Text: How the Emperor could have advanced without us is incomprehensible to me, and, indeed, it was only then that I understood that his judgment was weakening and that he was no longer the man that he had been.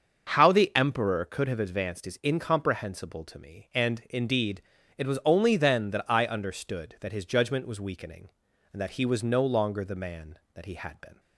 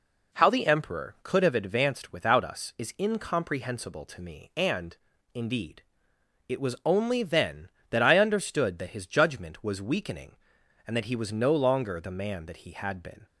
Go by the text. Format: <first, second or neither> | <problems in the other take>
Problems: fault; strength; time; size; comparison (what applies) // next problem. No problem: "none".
second | starts louder than the rest; until 1.3 s; 6.5 dB // skips "without us"; at 2.0 s